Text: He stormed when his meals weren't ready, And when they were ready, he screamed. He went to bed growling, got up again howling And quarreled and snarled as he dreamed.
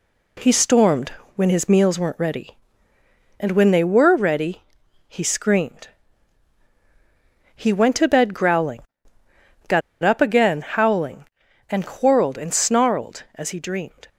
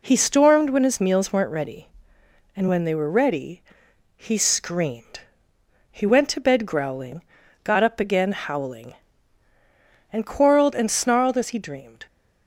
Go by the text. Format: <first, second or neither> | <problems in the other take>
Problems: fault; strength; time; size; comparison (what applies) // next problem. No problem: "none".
second | pauses between "stormed" and "when"; slight; at 1.0 s; 0.24 s long // pauses between "got" and "up"; slight; at 9.8 s; 0.22 s long